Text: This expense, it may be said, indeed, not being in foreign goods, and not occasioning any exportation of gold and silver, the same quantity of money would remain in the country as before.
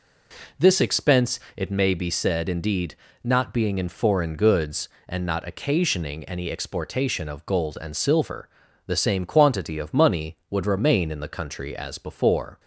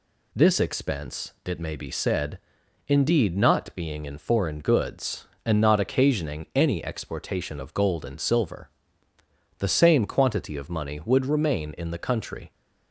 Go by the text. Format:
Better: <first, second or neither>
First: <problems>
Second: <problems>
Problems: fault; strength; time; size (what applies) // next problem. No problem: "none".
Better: first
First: none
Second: stops before "as before"; at 12.5 s